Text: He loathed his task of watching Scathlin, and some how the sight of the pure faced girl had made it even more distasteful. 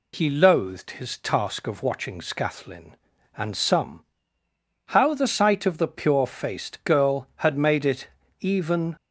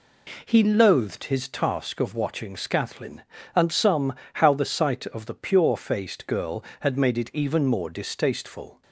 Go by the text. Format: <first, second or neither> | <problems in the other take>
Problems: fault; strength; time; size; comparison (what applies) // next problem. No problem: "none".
second | pauses between "some" and "how"; noticeable; at 4.0 s; 0.90 s long; slight in the second // pauses between "it" and "even"; slight; at 8.0 s; 0.32 s long // stops before "more distasteful"; at 8.9 s